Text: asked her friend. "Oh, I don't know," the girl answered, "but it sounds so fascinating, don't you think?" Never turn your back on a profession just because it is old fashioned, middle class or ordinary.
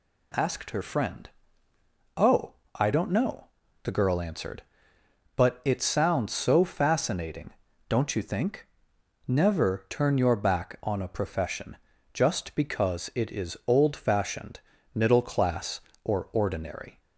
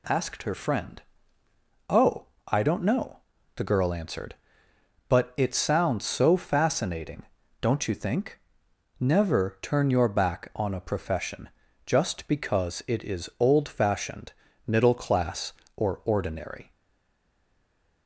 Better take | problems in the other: first | pauses between "profession" and "just"; at 11.4 s; 0.38 s long; also in the first // stays silent after the last word; noticeable; from 16.7 s on; 1.3 s long

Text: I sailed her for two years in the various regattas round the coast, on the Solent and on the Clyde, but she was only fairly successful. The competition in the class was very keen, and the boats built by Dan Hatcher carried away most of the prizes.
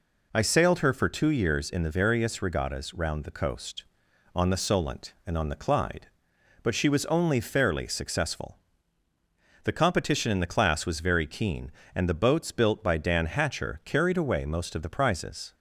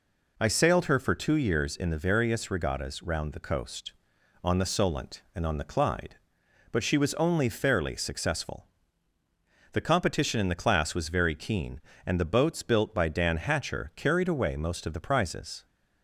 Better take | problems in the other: neither | none

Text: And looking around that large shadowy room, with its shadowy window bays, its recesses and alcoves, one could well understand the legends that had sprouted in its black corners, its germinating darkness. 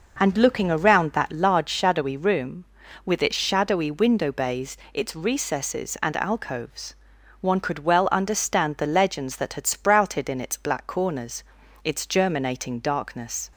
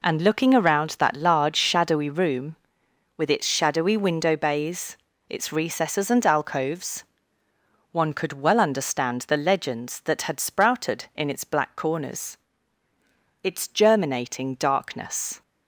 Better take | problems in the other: neither | none

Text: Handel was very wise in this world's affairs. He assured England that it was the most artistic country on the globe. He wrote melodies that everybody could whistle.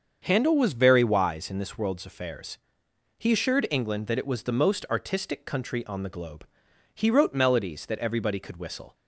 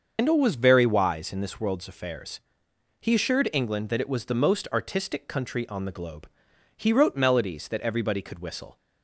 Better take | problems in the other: first | loses the start of "Handel"; at 0.1 s; 140 ms // starts louder than the rest; until 1.1 s; 6.5 dB; also in the first

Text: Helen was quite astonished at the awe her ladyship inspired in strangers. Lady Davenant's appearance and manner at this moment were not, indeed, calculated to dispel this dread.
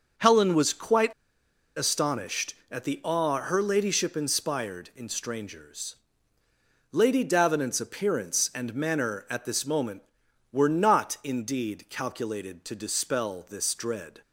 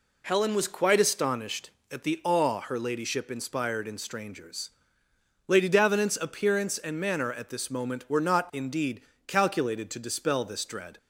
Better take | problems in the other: second | starts louder than the rest; noticeable; until 1.8 s; 6 dB // pauses between "quite" and "astonished"; noticeable; at 1.1 s; 0.63 s long

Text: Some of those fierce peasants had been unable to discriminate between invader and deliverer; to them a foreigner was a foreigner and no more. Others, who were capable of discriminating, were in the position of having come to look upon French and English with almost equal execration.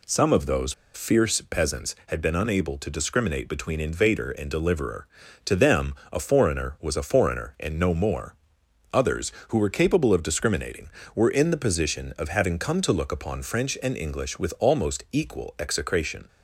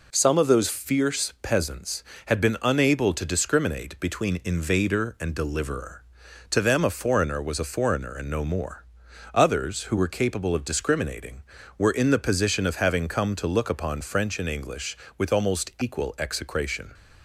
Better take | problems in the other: second | pauses between "those" and "fierce"; slight; at 0.7 s; 0.20 s long // pauses between "them" and "a"; slight; at 5.9 s; 0.18 s long

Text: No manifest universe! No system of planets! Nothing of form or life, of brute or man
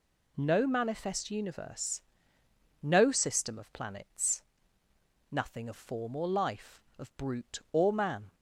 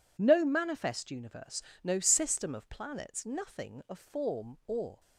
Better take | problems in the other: first | stops before "life of brute or man"; at 4.9 s

